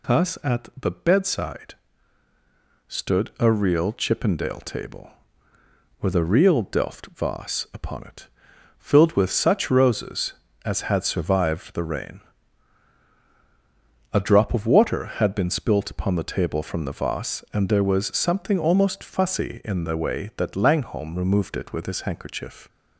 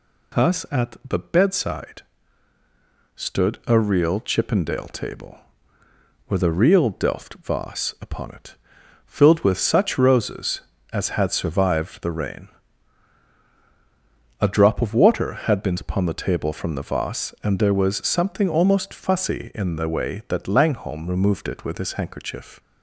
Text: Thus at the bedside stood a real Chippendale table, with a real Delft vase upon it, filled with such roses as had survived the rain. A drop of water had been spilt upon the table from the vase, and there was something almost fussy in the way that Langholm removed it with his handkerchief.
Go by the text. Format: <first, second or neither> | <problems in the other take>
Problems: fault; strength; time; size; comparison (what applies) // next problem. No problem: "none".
first | pauses between "bedside" and "stood"; at 2.0 s; 1.1 s long; also in the first // skips "spilt"; at 15.7 s